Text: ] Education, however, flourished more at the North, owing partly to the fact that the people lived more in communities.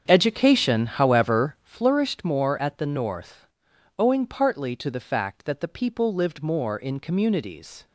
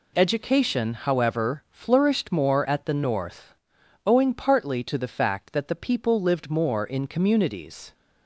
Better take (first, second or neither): second